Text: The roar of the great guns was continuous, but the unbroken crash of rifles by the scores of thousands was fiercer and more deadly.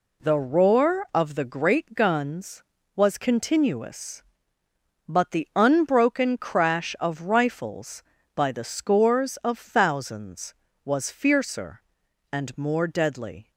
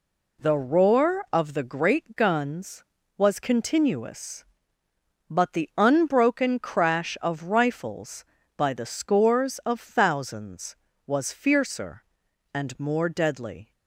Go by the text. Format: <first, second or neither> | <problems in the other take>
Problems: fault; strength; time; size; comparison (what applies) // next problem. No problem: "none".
neither | none